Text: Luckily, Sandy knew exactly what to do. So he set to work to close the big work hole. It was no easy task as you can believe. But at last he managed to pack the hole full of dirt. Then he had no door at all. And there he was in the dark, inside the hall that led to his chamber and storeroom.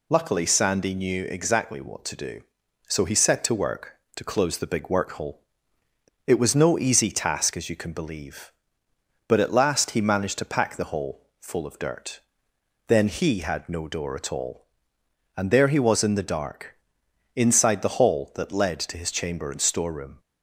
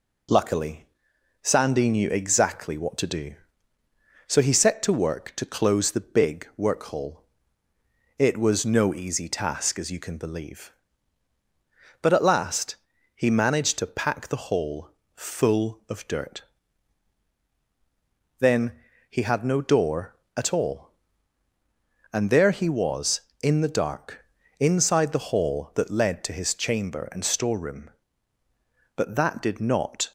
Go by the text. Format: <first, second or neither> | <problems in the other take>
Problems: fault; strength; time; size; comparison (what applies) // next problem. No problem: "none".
first | pauses between "last" and "he"; at 12.7 s; 0.40 s long // pauses between "hole" and "full"; slight; at 14.8 s; 0.26 s long // pauses between "Then" and "he"; slight; at 18.7 s; 0.36 s long // goes on to say "But that did not"; noticeable; from 28.9 s on; 1.1 s long